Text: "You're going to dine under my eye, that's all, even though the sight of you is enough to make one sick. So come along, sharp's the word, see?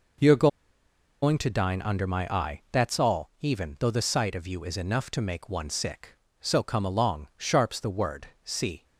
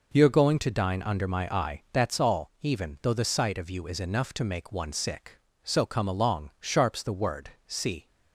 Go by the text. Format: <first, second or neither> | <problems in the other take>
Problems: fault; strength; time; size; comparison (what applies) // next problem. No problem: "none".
second | pauses between "You're" and "going"; noticeable; at 0.4 s; 0.75 s long